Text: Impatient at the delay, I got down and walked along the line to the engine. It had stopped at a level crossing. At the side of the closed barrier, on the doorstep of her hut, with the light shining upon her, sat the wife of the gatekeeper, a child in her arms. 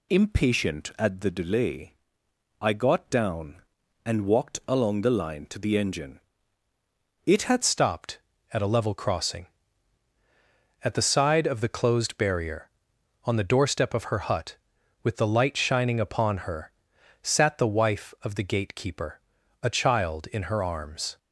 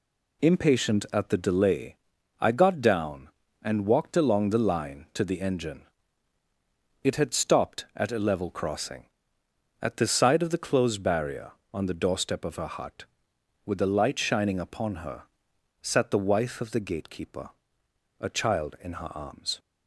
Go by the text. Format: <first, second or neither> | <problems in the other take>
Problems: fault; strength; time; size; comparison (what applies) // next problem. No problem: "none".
second | changes voice at "stopped"; from 7.6 s on; 13.5 s long